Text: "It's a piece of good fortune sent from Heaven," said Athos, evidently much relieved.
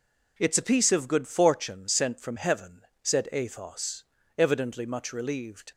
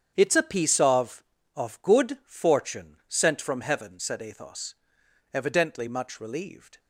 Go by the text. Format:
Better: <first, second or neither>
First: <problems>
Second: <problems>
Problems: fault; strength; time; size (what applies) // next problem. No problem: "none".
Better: first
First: none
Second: starts louder than the rest; strong; until 1.1 s; 8 dB // says "of" twice; at 1.5 s